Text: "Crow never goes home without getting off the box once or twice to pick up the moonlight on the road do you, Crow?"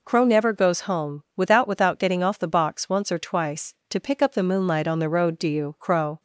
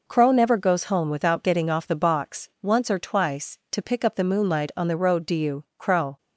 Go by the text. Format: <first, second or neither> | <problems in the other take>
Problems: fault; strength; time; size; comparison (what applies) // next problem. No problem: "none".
second | says "without" twice; at 1.6 s